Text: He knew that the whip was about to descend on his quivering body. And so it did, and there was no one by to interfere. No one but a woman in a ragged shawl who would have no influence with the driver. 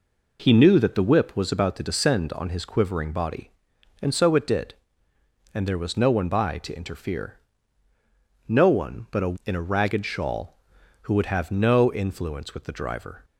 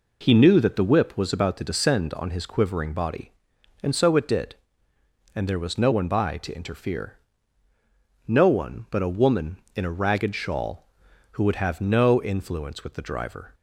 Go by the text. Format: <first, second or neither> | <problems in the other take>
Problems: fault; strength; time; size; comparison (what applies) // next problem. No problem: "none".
second | skips "woman"; at 9.4 s